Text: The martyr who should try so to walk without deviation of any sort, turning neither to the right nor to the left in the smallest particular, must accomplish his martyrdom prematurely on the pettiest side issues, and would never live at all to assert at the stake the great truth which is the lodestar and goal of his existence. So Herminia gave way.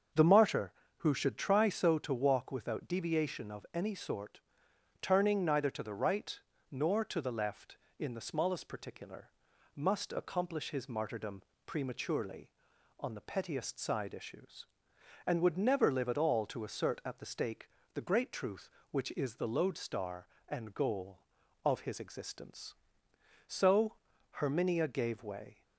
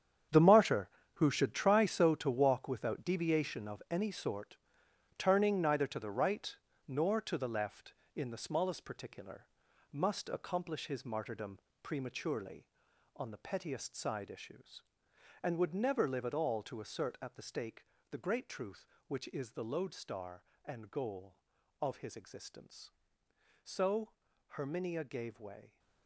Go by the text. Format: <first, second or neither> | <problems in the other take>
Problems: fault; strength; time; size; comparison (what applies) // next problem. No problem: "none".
first | gets quieter; strong; throughout; 12.5 dB // starts louder than the rest; strong; until 1.5 s; 8.5 dB; also in the first // pauses between "right" and "nor"; slight; at 6.5 s; 0.32 s long; slight in the first // pauses between "martyrdom" and "prematurely"; slight; at 11.5 s; 0.22 s long; slight in the first // pauses between "stake" and "the"; slight; at 17.8 s; 0.26 s long; slight in the first // pauses between "So" and "Herminia"; at 24.1 s; 0.38 s long; also in the first